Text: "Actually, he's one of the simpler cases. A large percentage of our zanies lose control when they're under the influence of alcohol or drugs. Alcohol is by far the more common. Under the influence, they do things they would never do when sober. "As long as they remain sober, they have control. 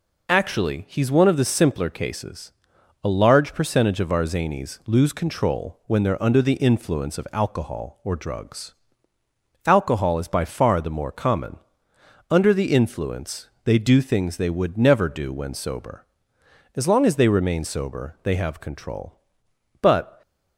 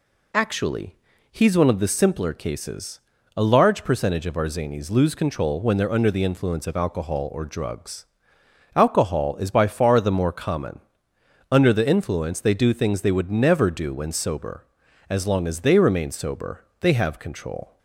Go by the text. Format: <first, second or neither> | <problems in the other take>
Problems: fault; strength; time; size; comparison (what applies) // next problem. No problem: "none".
second | goes on to say "But"; slight; from 19.8 s on; 0.40 s long